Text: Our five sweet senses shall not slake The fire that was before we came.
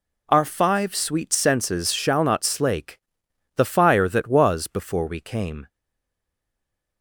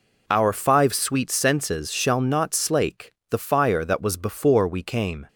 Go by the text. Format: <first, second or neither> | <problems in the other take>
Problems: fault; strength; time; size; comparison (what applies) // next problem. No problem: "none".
second | pauses between "slake" and "The"; noticeable; at 2.9 s; 0.57 s long; slight in the second // stays silent after the last word; noticeable; from 5.6 s on; 1.4 s long